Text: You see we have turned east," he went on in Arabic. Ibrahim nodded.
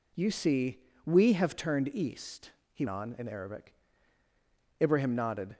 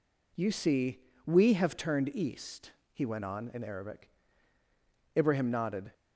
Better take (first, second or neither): second